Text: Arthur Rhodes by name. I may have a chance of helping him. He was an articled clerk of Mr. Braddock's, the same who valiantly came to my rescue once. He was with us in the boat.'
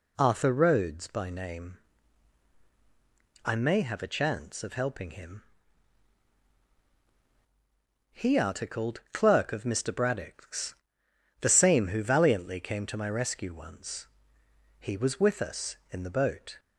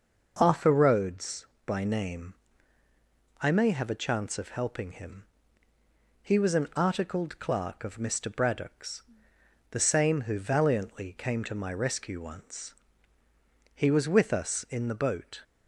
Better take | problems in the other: second | skips "was an"; at 8.3 s

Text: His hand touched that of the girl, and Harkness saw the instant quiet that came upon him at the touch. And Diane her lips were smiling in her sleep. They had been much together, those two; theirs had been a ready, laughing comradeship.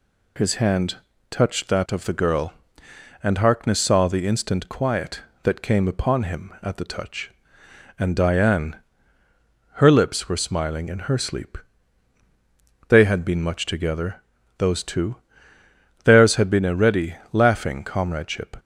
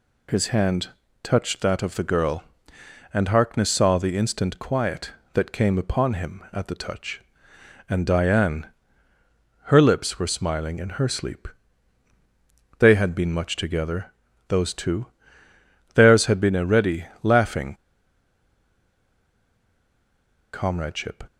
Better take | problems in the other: first | pauses between "hand" and "touched"; slight; at 0.8 s; 0.34 s long; slight in the first // pauses between "Diane" and "her"; noticeable; at 8.6 s; 0.96 s long; noticeable in the first // pauses between "laughing" and "comradeship"; strong; at 17.7 s; 2.7 s long

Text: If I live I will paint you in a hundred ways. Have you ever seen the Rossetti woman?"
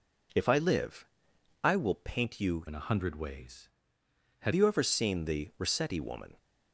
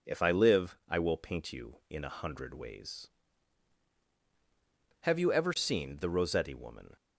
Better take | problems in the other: second | pauses between "live" and "I"; noticeable; at 1.0 s; 0.58 s long // changes voice from "in" to "Have"; from 2.6 to 4.5 s; 1.9 s long

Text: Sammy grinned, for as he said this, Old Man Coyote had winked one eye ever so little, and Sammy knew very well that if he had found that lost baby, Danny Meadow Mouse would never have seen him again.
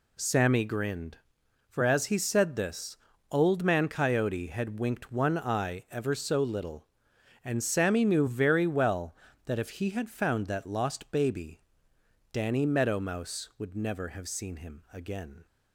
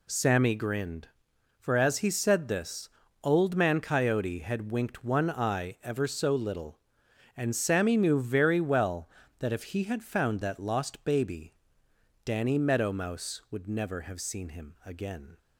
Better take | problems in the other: neither | none

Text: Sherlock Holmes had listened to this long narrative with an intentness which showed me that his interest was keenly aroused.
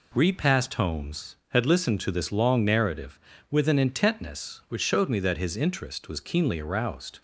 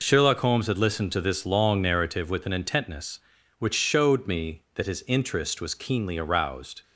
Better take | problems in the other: second | says "Repassed" for "Sherlock"; at 0.1 s

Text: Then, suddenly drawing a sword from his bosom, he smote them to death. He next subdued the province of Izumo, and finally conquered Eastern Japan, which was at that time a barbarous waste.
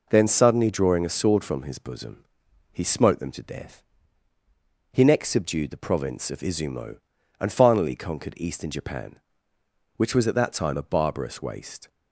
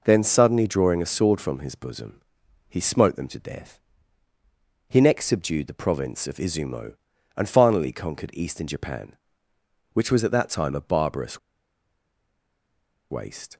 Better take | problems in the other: first | pauses between "barbarous" and "waste"; strong; at 11.3 s; 1.7 s long

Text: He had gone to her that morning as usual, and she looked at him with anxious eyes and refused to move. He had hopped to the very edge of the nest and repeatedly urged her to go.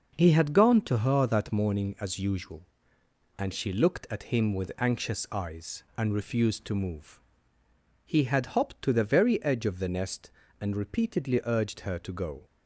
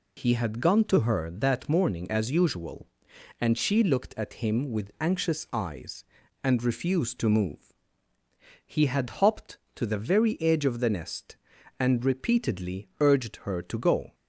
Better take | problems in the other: neither | none

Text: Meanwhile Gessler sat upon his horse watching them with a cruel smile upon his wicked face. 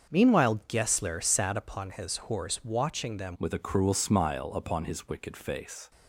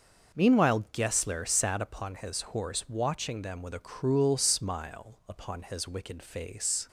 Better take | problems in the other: second | starts louder than the rest; until 1.1 s; 6.5 dB; noticeable in the second // changes voice at "with"; from 3.3 s on; 2.6 s long

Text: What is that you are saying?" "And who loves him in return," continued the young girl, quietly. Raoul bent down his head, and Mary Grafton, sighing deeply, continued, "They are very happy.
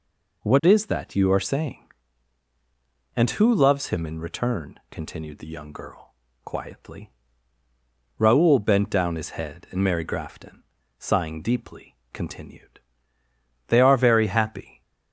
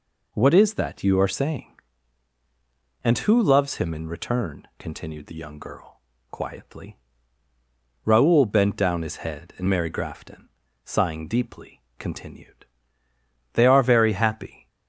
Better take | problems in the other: neither | none

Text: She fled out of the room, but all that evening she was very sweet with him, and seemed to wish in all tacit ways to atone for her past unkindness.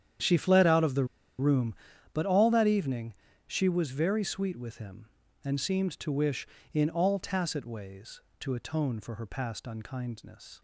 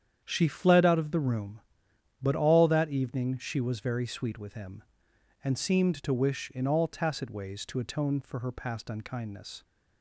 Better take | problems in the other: second | starts louder than the rest; strong; until 1.5 s; 9 dB; strong in the second // pauses between "the" and "room"; slight; at 1.0 s; 0.33 s long // pauses between "evening" and "she"; slight; at 3.1 s; 0.32 s long

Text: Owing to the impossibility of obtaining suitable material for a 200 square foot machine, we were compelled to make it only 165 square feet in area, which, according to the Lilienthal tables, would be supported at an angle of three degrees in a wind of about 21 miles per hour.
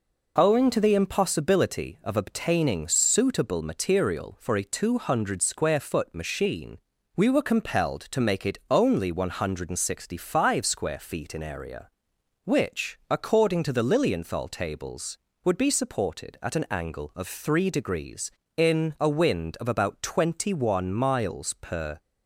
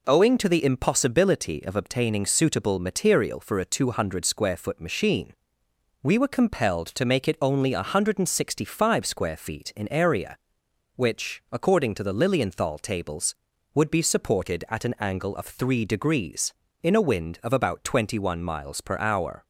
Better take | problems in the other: second | stops before "hour"; at 21.9 s

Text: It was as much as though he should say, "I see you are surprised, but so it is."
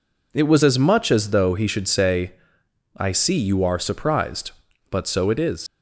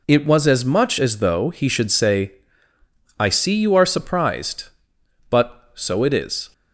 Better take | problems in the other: second | leaves "is" unfinished; at 5.6 s; 125 ms

